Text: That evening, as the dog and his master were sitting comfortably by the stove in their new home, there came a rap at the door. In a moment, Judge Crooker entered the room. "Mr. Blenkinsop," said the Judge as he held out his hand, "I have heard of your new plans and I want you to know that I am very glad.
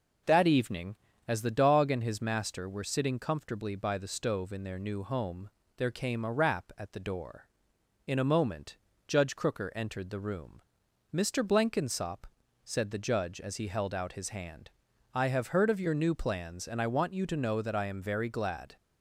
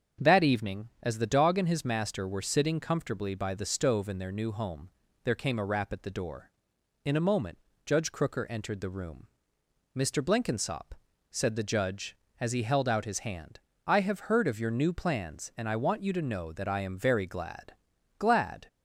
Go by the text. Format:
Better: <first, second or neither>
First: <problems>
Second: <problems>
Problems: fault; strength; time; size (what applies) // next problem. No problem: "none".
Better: first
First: none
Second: starts louder than the rest; until 1.3 s; 7 dB // says "glad" twice; at 18.1 s